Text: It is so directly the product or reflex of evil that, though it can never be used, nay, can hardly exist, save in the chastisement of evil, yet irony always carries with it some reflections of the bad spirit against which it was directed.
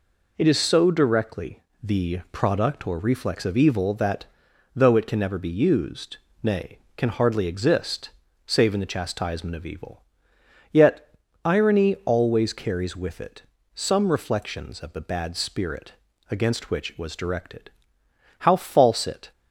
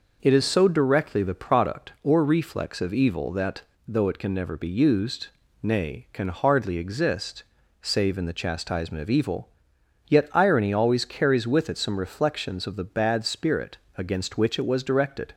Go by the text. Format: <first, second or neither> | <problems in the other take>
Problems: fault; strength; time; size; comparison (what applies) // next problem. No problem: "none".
second | pauses between "directly" and "the"; slight; at 1.6 s; 0.22 s long // pauses between "yet" and "irony"; slight; at 11.0 s; 0.34 s long // pauses between "it" and "some"; slight; at 13.4 s; 0.32 s long // pauses between "spirit" and "against"; at 15.9 s; 0.38 s long; slight in the second // goes on to say "How false it"; noticeable; from 18.3 s on; 0.92 s long